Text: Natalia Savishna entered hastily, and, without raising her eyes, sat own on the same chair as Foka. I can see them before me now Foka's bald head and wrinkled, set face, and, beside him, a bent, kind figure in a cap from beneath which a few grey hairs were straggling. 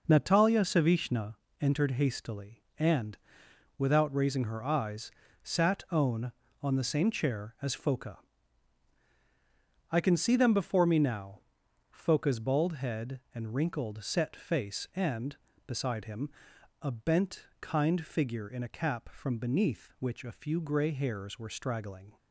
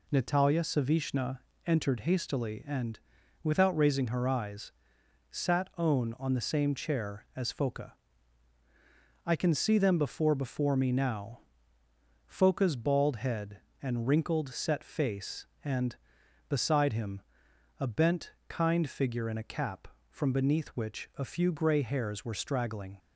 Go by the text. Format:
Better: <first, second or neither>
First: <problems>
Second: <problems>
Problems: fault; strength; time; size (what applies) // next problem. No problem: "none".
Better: first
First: pauses between "Savishna" and "entered"; slight; at 1.3 s; 0.26 s long // pauses between "now" and "Foka's"; noticeable; at 11.3 s; 0.50 s long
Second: pauses between "Savishna" and "entered"; slight; at 1.4 s; 0.26 s long // says "before" twice; at 10.3 s // pauses between "now" and "Foka's"; noticeable; at 11.4 s; 0.86 s long